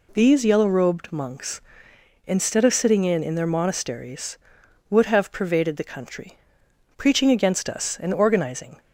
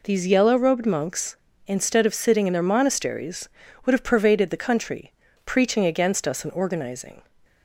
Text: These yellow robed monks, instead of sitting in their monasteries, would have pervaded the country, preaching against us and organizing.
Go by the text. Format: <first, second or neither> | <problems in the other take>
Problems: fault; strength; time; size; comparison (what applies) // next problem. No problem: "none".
second | says "in" twice; at 3.2 s